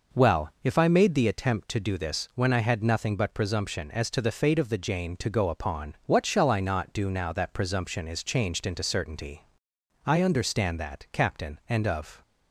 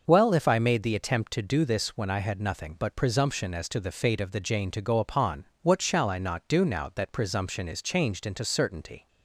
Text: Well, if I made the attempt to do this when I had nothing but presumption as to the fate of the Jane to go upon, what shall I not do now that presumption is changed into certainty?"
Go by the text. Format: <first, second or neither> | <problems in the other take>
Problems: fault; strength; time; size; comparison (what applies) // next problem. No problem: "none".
second | goes on to say "I understand that captain and of"; strong; from 10.0 s on; 2.1 s long